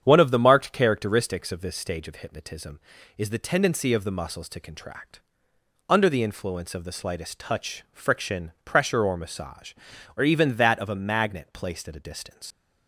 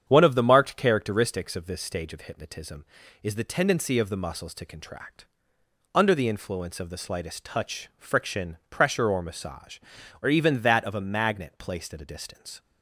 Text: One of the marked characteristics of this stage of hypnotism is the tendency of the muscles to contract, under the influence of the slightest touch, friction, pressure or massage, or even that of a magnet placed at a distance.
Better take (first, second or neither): second